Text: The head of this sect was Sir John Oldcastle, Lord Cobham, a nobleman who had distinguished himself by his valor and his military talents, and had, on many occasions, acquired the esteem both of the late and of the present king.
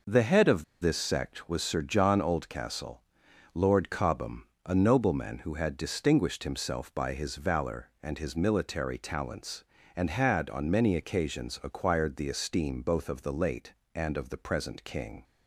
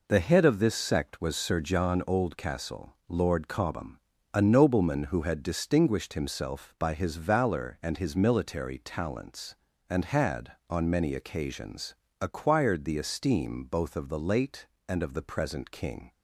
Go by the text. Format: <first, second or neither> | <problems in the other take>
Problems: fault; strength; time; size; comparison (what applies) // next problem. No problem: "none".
second | pauses between "of" and "this"; slight; at 0.6 s; 0.17 s long